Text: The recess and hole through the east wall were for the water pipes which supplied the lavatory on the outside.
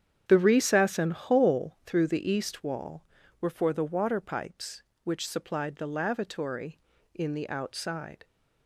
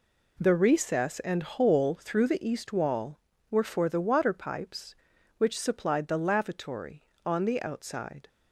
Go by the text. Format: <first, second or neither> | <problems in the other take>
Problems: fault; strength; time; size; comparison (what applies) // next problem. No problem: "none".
second | starts louder than the rest; strong; until 1.2 s; 8.5 dB // says "in" for "on"; at 7.1 s